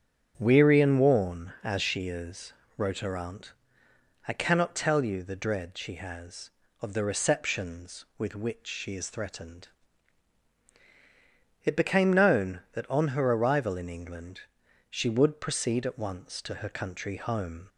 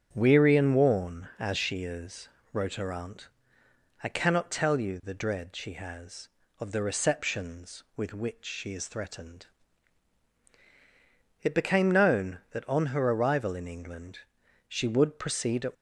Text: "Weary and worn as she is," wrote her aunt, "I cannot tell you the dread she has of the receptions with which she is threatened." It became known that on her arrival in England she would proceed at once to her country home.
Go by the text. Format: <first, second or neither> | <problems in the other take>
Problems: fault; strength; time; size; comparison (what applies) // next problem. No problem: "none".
first | starts louder than the rest; strong; until 1.1 s; 7.5 dB; strong in the first // pauses between "England" and "she"; noticeable; at 14.2 s; 0.48 s long; noticeable in the first // stops before "once to her country home"; at 15.7 s